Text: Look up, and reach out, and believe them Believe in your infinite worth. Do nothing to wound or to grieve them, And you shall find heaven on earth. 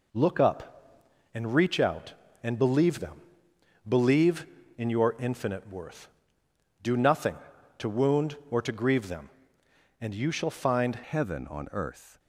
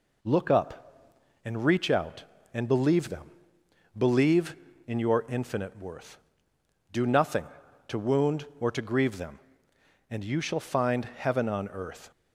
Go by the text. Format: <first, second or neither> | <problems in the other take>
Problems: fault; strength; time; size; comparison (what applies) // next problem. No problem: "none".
second | pauses between "them" and "Believe"; noticeable; at 3.1 s; 0.68 s long; noticeable in the second // changes voice at "heaven"; from 11.0 s on; 1.1 s long